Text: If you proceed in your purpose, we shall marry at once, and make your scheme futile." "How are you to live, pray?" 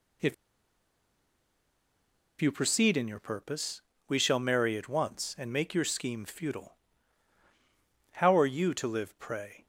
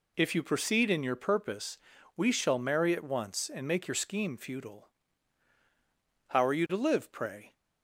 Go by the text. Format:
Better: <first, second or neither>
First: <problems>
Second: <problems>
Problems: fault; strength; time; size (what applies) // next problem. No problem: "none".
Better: second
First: pauses between "If" and "you"; strong; at 0.3 s; 2.0 s long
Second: none